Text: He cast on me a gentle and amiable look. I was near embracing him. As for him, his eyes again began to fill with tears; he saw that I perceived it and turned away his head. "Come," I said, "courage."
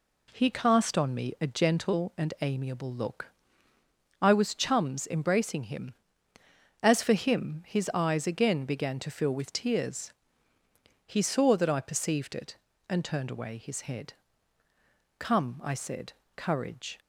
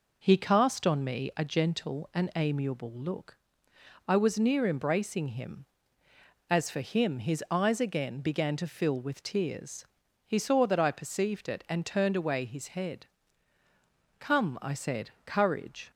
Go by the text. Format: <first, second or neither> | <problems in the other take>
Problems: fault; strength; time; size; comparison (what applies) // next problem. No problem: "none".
second | says "chums" for "near"; at 4.5 s